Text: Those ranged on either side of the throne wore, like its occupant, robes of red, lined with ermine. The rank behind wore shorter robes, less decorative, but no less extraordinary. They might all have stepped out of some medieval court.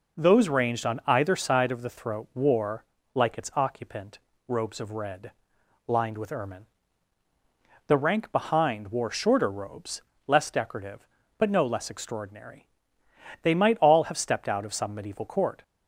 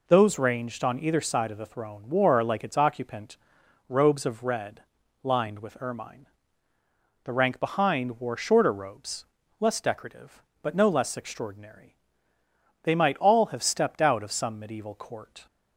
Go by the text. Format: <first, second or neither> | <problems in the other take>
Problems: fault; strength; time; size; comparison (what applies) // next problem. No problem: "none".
second | says "throat" for "throne"; at 1.8 s